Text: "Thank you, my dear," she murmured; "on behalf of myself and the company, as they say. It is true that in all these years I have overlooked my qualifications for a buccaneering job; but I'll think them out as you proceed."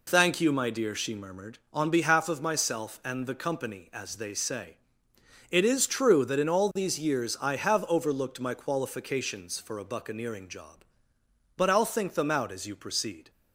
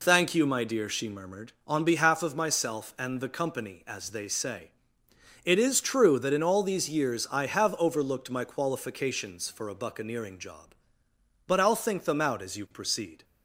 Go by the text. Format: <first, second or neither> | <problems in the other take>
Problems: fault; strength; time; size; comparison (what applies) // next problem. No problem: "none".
neither | none